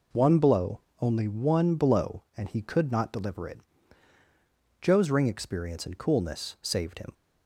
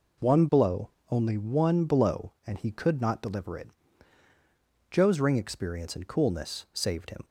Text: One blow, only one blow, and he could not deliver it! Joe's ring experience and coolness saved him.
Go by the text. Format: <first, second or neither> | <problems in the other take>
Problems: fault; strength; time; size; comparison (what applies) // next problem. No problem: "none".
neither | none